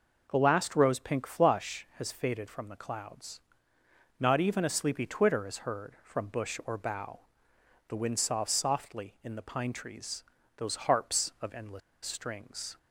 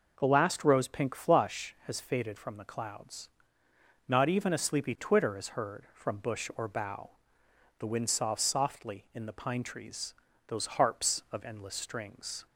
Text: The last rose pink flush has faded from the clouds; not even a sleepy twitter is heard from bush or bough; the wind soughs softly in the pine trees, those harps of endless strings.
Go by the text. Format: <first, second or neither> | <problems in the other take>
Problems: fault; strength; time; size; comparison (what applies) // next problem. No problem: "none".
second | pauses between "endless" and "strings"; slight; at 11.8 s; 0.25 s long